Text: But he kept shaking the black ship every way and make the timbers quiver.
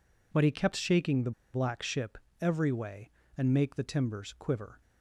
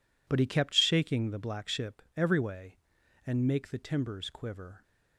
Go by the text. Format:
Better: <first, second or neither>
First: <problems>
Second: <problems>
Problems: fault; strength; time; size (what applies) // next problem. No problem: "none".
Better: second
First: pauses between "the" and "black"; slight; at 1.3 s; 0.22 s long // pauses between "ship" and "every"; slight; at 2.1 s; 0.22 s long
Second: none